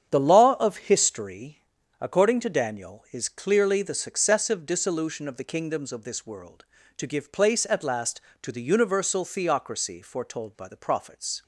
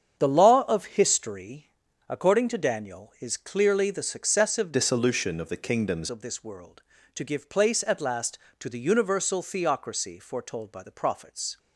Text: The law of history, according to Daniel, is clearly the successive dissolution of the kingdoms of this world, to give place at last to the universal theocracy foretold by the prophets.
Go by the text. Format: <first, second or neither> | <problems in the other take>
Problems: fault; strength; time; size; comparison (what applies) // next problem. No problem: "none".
first | starts louder than the rest; strong; until 1.1 s; 8 dB; strong in the first // changes voice from "dissolution" to "kingdoms"; from 4.7 to 6.0 s; 1.3 s long